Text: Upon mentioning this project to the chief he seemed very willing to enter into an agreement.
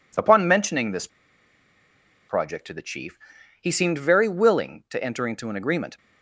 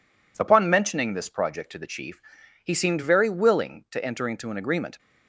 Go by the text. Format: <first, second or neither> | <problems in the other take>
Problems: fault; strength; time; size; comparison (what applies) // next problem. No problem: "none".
second | pauses between "this" and "project"; at 1.0 s; 1.2 s long // pauses between "chief" and "he"; at 3.1 s; 0.44 s long; also in the second